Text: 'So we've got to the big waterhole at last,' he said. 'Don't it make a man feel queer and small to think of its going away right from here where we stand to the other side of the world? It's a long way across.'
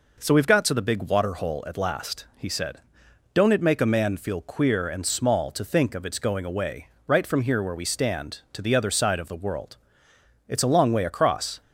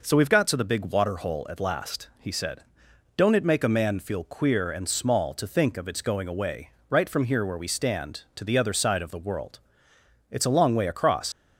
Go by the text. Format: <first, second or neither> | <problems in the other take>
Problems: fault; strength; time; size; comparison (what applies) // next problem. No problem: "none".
first | pauses between "away" and "right"; slight; at 6.7 s; 0.18 s long; slight in the first // leaves "across" unfinished; at 11.3 s; 115 ms